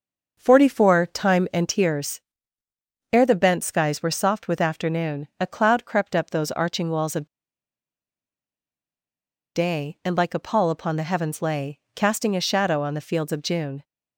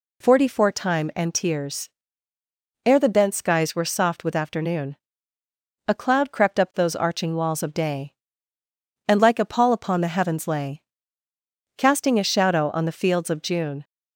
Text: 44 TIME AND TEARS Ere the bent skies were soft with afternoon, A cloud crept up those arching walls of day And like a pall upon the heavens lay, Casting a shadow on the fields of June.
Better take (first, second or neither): second